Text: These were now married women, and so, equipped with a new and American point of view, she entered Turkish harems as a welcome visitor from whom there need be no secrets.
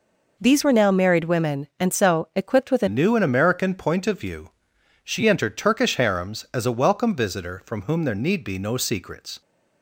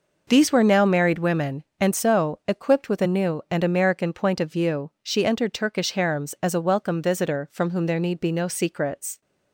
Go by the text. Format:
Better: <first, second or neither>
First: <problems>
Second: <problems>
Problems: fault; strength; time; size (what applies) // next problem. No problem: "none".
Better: second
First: changes voice at "new"; from 2.8 s on; 6.6 s long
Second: none